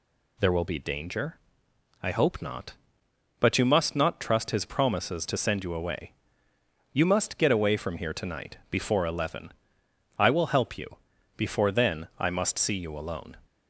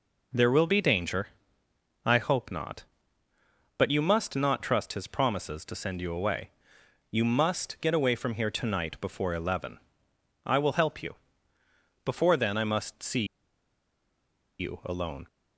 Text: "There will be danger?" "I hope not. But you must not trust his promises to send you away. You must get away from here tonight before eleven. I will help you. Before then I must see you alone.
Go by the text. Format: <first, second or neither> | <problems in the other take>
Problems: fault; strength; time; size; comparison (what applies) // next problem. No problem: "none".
first | pauses between "see" and "you"; strong; at 13.2 s; 1.3 s long